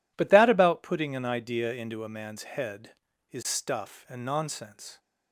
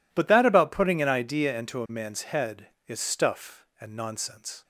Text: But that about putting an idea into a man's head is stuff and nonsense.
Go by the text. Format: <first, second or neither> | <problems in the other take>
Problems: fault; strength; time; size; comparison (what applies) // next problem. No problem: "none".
neither | none